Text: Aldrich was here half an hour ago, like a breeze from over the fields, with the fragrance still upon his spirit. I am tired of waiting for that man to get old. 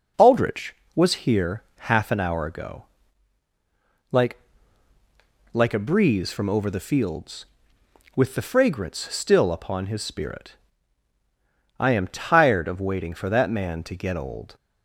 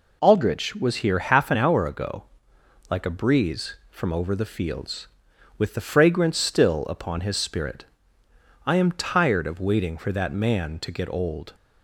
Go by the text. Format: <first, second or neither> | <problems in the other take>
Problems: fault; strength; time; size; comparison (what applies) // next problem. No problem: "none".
second | says "like" twice; at 5.5 s